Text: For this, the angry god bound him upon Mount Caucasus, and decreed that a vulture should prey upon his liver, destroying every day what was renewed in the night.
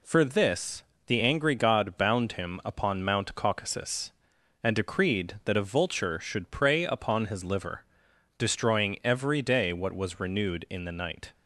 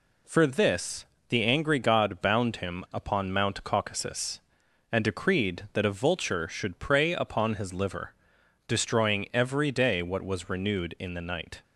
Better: neither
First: none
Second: none

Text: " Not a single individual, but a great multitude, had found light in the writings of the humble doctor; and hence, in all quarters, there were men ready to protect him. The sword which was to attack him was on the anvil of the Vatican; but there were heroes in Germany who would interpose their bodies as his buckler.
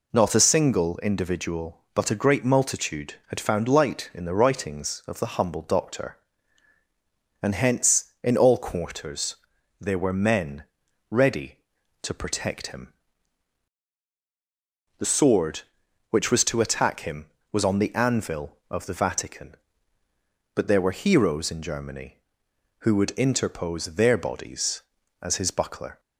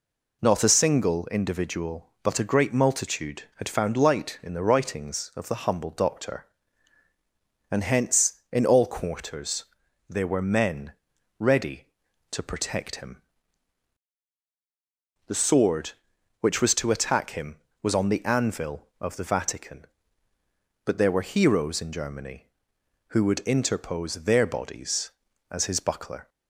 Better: neither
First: pauses between "men" and "ready"; at 10.6 s; 0.44 s long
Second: pauses between "men" and "ready"; at 10.9 s; 0.44 s long

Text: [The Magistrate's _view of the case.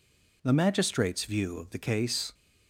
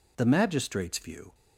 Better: first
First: none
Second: stops before "of the case"; at 1.3 s

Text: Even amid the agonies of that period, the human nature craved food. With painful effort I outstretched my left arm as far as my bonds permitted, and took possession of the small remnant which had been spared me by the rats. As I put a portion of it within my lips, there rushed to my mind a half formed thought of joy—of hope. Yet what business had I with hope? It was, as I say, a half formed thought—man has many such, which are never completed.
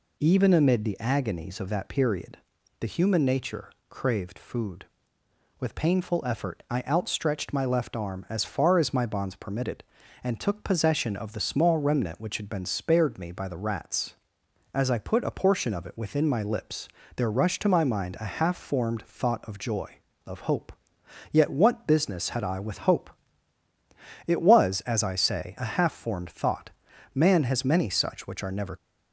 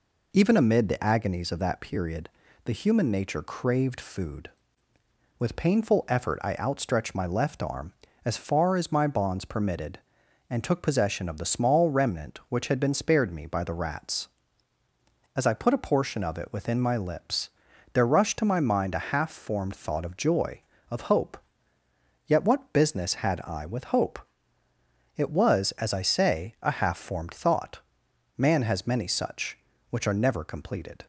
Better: second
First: pauses between "nature" and "craved"; slight; at 3.6 s; 0.20 s long // stops before "completed"; at 28.7 s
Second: none

